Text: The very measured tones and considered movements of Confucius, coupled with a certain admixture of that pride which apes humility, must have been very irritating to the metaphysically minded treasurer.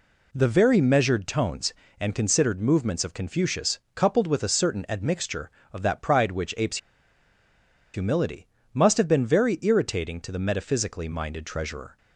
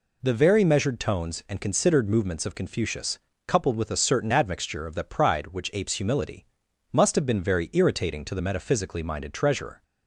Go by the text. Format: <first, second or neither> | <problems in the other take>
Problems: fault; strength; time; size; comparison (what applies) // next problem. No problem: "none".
second | pauses between "apes" and "humility"; at 6.7 s; 1.1 s long